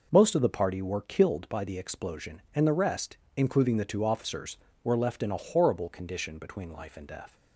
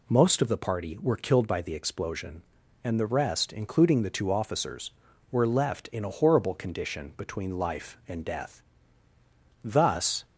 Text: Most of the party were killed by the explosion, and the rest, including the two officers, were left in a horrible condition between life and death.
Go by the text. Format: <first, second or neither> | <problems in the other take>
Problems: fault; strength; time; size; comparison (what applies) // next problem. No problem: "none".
first | goes on to say "Thus"; noticeable; from 9.6 s on; 0.62 s long